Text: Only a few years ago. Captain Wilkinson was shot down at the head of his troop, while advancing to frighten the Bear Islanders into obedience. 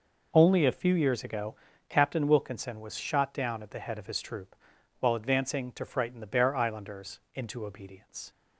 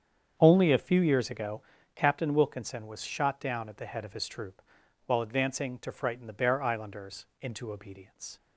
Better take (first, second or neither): first